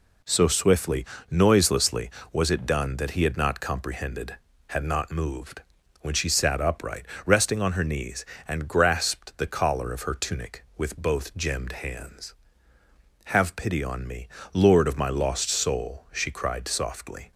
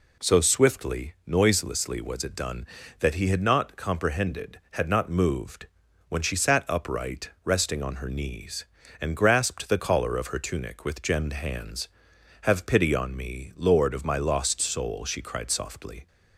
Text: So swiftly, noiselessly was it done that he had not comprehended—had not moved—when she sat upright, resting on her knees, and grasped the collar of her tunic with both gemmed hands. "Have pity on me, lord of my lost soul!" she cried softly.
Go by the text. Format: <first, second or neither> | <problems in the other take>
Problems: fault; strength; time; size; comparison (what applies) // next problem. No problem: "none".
first | skips "both"; at 11.0 s